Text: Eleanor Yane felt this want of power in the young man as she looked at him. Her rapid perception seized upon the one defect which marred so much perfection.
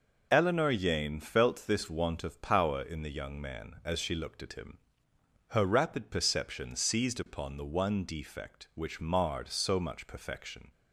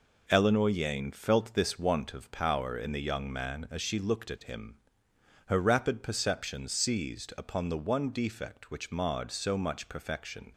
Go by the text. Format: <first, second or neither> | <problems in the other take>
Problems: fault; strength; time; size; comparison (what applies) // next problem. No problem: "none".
neither | none